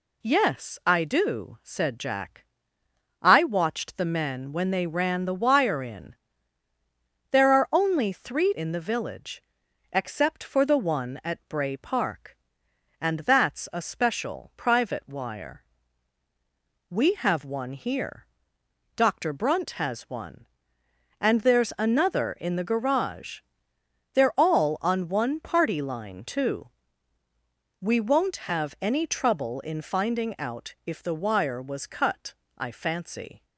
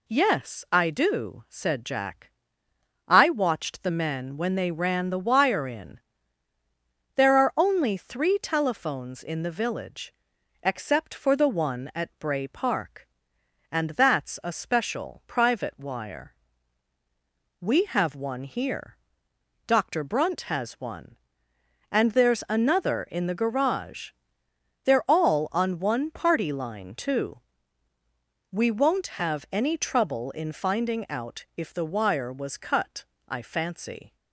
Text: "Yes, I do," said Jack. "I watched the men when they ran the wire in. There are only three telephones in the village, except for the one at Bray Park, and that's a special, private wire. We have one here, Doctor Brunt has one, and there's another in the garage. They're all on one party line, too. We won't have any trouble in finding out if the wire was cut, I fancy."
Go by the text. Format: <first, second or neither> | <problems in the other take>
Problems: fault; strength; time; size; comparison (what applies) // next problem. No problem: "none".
second | skips "telephones"; at 8.5 s